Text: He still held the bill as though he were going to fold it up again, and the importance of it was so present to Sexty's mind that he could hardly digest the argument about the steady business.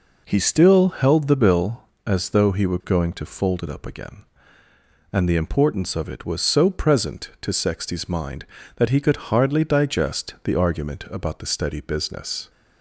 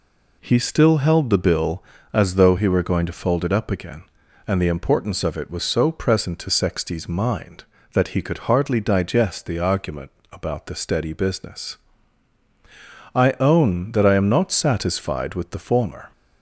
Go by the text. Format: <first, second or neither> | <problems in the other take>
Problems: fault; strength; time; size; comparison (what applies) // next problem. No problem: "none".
first | pauses between "argument" and "about"; slight; at 10.1 s; 0.20 s long // goes on to say "I own that I am not satisfied with the former"; strong; from 13.1 s on; 2.9 s long